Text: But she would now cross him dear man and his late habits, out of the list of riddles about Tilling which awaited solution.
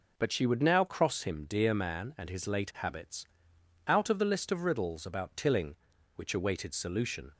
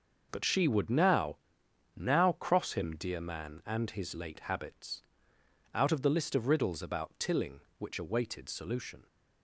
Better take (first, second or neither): first